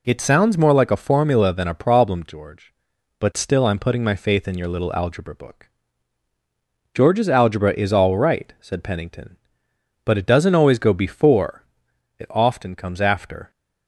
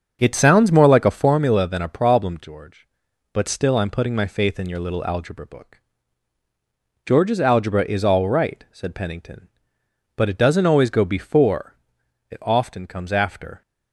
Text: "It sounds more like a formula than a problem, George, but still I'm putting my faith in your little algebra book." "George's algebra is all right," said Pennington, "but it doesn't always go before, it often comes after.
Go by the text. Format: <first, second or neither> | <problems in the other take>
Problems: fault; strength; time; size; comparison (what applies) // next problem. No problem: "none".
first | starts louder than the rest; until 1.5 s; 7 dB